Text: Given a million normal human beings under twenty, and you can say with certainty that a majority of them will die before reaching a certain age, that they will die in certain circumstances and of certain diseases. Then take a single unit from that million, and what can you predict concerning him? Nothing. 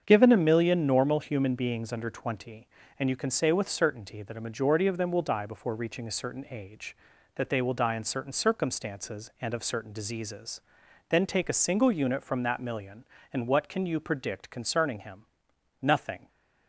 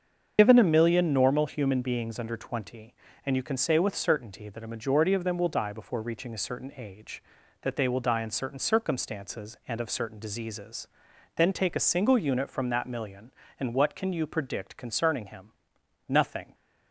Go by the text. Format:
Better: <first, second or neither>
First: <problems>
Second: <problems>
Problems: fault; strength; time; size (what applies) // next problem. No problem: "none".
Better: first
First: starts louder than the rest; strong; until 1.0 s; 7.5 dB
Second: loses the start of "Given"; at 0.3 s; 70 ms // starts louder than the rest; until 1.3 s; 7 dB